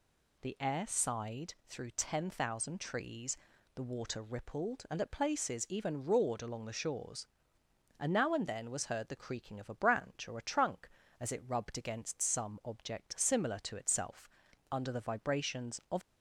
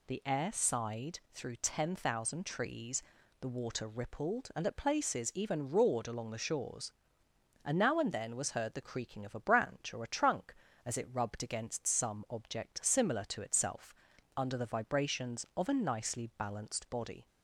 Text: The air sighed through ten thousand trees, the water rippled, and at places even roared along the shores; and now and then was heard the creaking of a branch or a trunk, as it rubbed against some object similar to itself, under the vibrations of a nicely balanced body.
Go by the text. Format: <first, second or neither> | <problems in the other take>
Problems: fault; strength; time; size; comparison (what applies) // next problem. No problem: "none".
second | stops before "a nicely balanced body"; at 16.0 s